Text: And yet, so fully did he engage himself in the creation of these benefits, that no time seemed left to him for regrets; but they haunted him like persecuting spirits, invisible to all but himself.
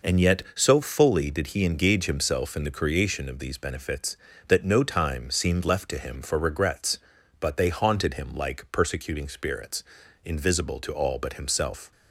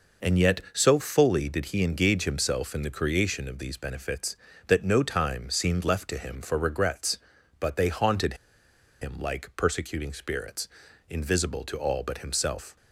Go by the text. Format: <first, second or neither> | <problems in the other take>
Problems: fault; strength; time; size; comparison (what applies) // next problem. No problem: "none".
first | pauses between "haunted" and "him"; noticeable; at 8.3 s; 0.66 s long